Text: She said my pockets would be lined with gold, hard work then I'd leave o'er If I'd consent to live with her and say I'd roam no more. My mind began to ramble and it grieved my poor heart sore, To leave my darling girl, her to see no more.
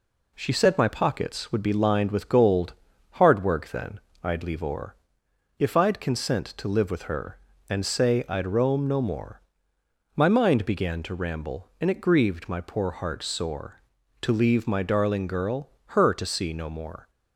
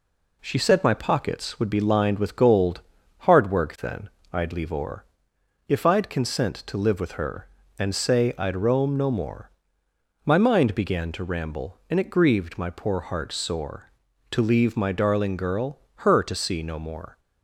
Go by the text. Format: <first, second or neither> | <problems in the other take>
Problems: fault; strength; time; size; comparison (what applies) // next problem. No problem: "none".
neither | pauses between "then" and "I'd"; slight; the same in both // pauses between "o'er" and "If"; noticeable; the same in both